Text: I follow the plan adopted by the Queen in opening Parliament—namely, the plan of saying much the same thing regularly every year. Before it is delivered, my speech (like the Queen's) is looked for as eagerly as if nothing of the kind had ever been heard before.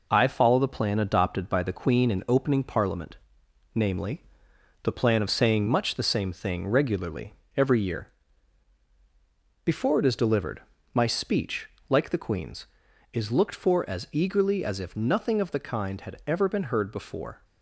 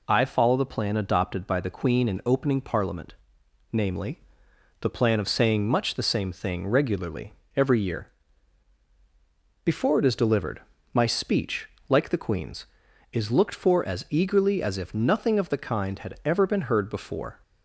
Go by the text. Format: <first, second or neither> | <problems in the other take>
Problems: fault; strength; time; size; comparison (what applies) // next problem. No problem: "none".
second | gets quieter; noticeable; throughout; 4.5 dB // pauses between "regularly" and "every"; slight; at 7.3 s; 0.22 s long; slight in the second